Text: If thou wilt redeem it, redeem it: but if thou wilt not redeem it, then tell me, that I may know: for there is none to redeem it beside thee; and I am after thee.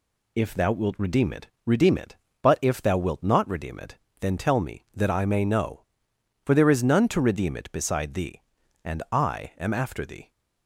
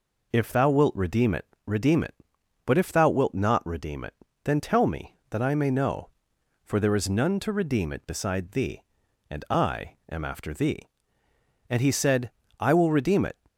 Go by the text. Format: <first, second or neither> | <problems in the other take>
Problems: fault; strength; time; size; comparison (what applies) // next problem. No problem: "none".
first | goes on to say "And he said I will redeem it"; from 11.6 s on; 1.6 s long